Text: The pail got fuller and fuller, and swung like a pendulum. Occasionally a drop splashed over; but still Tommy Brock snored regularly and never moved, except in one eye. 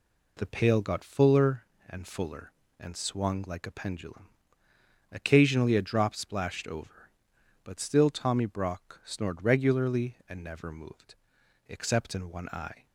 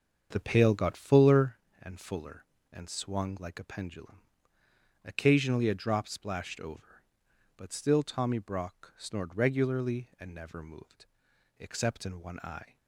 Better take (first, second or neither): first